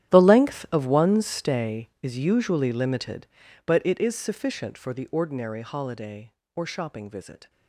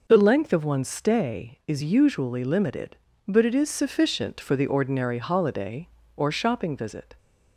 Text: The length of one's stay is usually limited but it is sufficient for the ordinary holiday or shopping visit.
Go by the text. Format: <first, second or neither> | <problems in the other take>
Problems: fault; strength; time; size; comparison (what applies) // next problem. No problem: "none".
second | gets quieter; strong; throughout; 17.5 dB